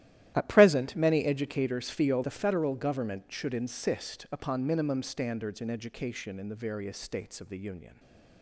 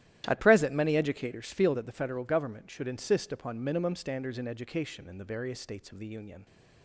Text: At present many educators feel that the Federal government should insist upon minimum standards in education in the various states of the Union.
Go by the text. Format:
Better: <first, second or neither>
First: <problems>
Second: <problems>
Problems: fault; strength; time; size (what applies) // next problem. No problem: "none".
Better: second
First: starts louder than the rest; strong; until 1.3 s; 13 dB // skips "that"; at 2.2 s // stays silent after the last word; slight; from 7.8 s on; 0.6 s long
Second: starts louder than the rest; strong; until 1.2 s; 13 dB